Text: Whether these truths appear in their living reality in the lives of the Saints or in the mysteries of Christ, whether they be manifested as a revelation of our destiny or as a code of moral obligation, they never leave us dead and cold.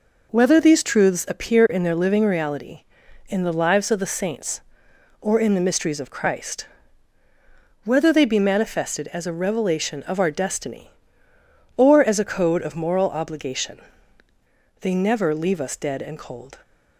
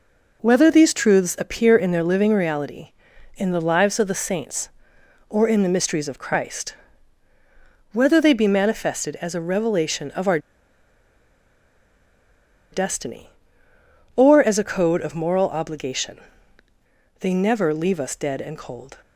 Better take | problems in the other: first | pauses between "our" and "destiny"; strong; at 10.3 s; 2.3 s long

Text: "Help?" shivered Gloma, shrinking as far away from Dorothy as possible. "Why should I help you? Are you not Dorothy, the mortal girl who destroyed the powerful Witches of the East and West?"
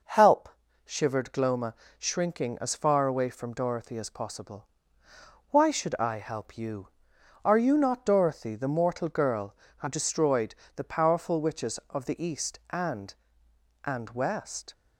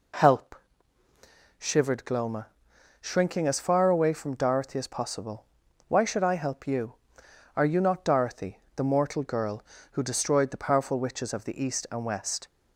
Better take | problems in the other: second | pauses between "destroyed" and "the"; slight; at 10.5 s; 0.22 s long // says "and" twice; at 13.8 s

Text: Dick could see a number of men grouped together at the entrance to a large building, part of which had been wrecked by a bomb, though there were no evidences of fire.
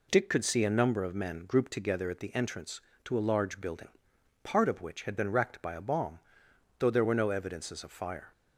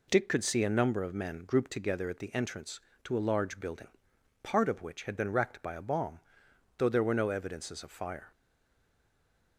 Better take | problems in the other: first | stays silent after the last word; noticeable; from 8.3 s on; 1.2 s long

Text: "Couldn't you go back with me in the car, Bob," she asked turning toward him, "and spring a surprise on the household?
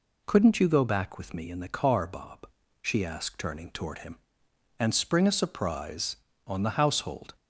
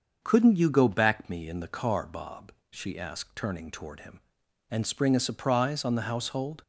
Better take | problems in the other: first | starts louder than the rest; until 1.2 s; 6.5 dB // skips "with"; at 1.2 s

